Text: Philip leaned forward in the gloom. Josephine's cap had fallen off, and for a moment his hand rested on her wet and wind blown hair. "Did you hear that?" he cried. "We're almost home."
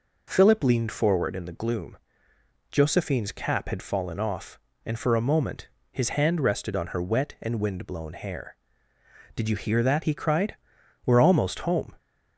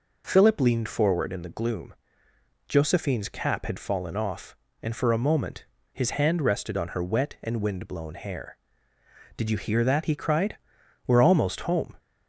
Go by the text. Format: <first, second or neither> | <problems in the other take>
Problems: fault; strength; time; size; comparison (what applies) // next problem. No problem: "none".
neither | pauses between "moment" and "his"; slight; the same in both